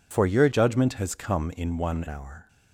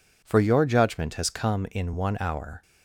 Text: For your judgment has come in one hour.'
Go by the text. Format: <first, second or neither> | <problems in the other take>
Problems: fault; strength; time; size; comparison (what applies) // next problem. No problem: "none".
second | changes voice from "judgment" to "one"; from 0.5 to 2.0 s; 1.5 s long